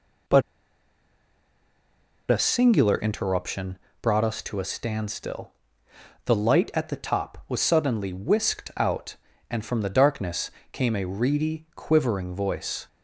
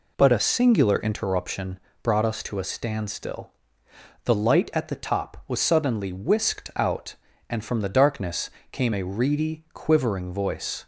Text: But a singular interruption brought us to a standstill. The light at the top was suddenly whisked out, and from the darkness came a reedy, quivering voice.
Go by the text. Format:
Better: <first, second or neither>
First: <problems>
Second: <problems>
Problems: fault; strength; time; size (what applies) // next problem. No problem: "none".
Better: second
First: pauses between "But" and "a"; strong; at 0.4 s; 1.8 s long // pauses between "interruption" and "brought"; slight; at 3.7 s; 0.24 s long // pauses between "darkness" and "came"; slight; at 10.4 s; 0.22 s long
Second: pauses between "interruption" and "brought"; slight; at 1.7 s; 0.24 s long // pauses between "darkness" and "came"; slight; at 8.4 s; 0.22 s long